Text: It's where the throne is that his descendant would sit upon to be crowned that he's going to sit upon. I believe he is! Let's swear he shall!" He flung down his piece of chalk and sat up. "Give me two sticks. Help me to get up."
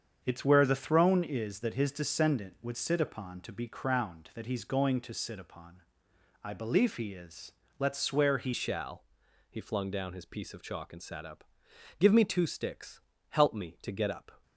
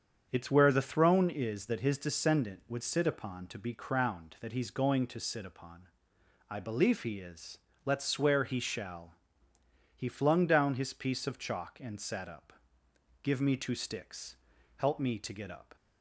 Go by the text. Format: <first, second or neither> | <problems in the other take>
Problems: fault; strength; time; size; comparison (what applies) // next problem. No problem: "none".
second | starts louder than the rest; strong; until 1.2 s; 7.5 dB; strong in the second // changes voice at "shall"; from 8.5 s on; 5.9 s long